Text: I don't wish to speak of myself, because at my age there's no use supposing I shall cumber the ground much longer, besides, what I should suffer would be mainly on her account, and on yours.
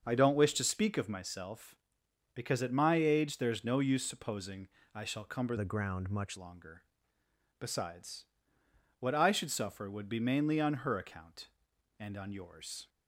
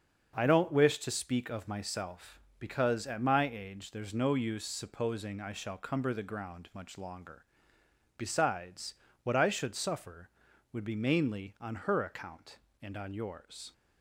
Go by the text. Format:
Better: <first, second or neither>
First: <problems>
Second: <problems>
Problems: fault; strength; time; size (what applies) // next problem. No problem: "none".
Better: second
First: starts louder than the rest; until 1.1 s; 6 dB // pauses between "supposing" and "I"; slight; at 4.6 s; 0.26 s long // changes voice from "the" to "much"; from 5.5 to 6.3 s; 0.8 s long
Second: starts louder than the rest; until 1.4 s; 6.5 dB